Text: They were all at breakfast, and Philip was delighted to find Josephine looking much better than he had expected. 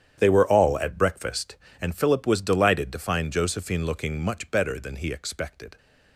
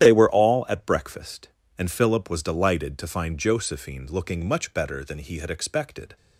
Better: second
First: starts louder than the rest; strong; until 1.2 s; 9.5 dB // skips "had"; at 5.1 s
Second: starts louder than the rest; strong; until 1.0 s; 11 dB

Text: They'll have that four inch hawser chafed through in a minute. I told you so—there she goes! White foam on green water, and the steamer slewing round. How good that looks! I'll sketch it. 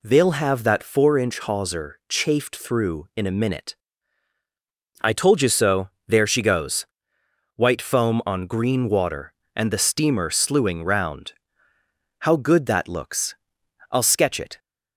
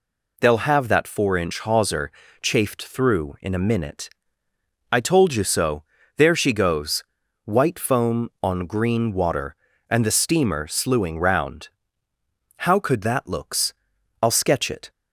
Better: first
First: none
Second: pauses between "hawser" and "chafed"; slight; at 2.1 s; 0.32 s long // says "could" for "good"; at 12.7 s

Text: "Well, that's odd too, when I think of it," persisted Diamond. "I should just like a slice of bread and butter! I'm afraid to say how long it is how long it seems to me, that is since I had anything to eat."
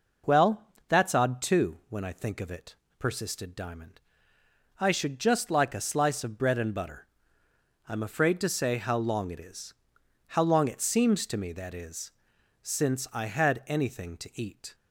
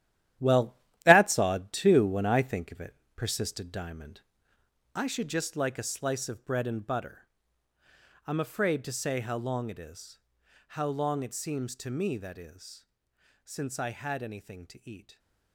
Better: first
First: pauses between "is" and "how"; noticeable; at 9.7 s; 0.54 s long // pauses between "is" and "since"; noticeable; at 12.1 s; 0.52 s long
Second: gets quieter; strong; throughout; 10 dB // pauses between "is" and "how"; noticeable; at 10.2 s; 0.52 s long // pauses between "is" and "since"; noticeable; at 12.8 s; 0.58 s long

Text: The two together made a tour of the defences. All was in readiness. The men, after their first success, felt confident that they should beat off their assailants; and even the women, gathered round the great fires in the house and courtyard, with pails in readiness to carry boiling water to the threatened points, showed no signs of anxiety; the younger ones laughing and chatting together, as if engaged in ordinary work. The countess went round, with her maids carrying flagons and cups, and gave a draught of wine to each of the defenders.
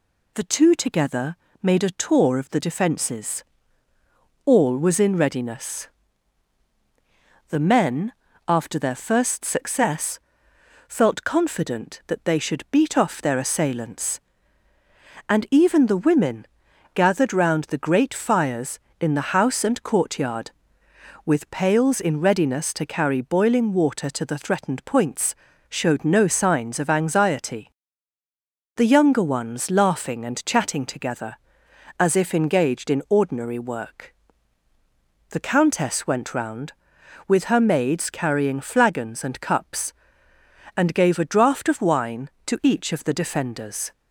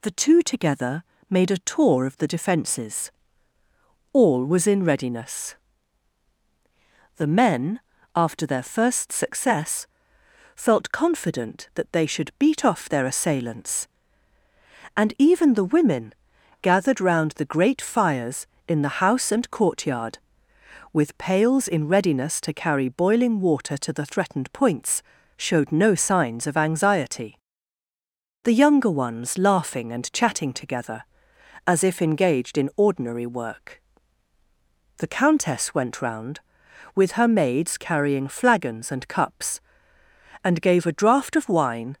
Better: first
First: pauses between "together" and "made"; slight; at 1.3 s; 0.26 s long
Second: pauses between "together" and "made"; slight; at 1.0 s; 0.26 s long // stops before "to each of the defenders"; at 41.9 s

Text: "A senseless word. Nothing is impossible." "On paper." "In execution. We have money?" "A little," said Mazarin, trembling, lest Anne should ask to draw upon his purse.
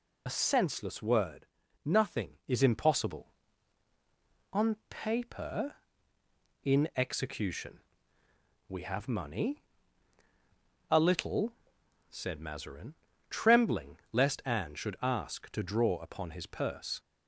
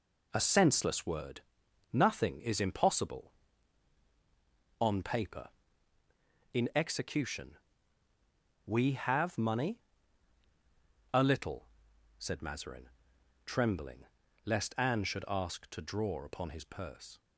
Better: second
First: loses the start of "A"; at 0.2 s; 35 ms // pauses between "On" and "paper"; slight; at 4.7 s; 0.16 s long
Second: none

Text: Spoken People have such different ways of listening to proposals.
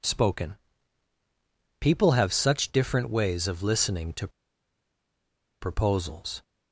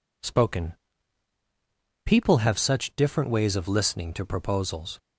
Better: second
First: pauses between "Spoken" and "People"; strong; at 0.5 s; 1.2 s long // pauses between "to" and "proposals"; strong; at 4.2 s; 1.3 s long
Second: pauses between "Spoken" and "People"; strong; at 0.7 s; 1.3 s long

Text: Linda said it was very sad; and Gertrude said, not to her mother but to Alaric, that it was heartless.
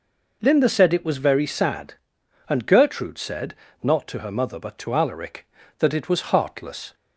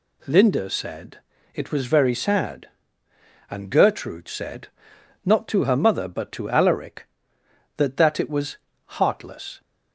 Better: first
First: none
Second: pauses between "said" and "it"; at 1.1 s; 0.38 s long // says "that" twice; at 7.9 s // pauses between "was" and "heartless"; slight; at 8.5 s; 0.30 s long

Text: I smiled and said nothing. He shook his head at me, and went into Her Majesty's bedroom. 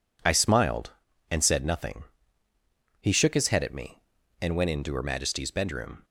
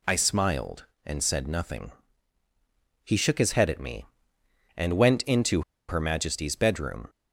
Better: first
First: none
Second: pauses between "into" and "Her"; slight; at 5.6 s; 0.26 s long

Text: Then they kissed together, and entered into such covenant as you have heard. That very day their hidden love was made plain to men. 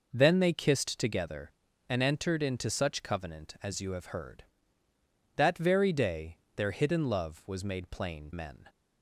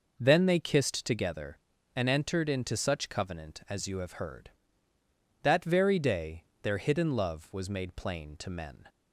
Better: second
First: pauses between "day" and "their"; slight; at 6.3 s; 0.18 s long // skips "to"; at 8.3 s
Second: pauses between "day" and "their"; slight; at 6.4 s; 0.18 s long

